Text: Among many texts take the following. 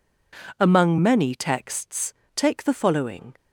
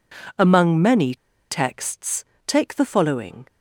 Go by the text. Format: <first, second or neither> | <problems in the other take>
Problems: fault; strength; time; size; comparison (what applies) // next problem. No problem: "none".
first | pauses between "many" and "texts"; slight; at 1.1 s; 0.34 s long // pauses between "texts" and "take"; slight; at 2.2 s; 0.22 s long; slight in the first